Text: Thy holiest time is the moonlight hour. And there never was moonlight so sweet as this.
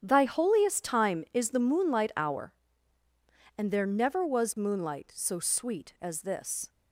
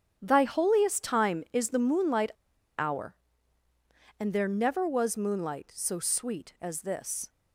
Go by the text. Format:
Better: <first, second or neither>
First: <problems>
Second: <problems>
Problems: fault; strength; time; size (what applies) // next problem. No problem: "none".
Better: first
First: starts louder than the rest; strong; until 1.0 s; 8.5 dB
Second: starts louder than the rest; strong; until 1.2 s; 8.5 dB // pauses between "moonlight" and "hour"; noticeable; at 2.3 s; 0.48 s long